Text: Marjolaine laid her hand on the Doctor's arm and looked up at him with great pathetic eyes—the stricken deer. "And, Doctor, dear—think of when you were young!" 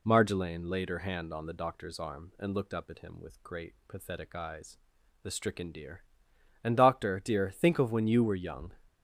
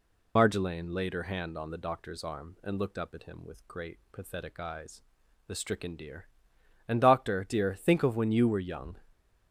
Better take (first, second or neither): first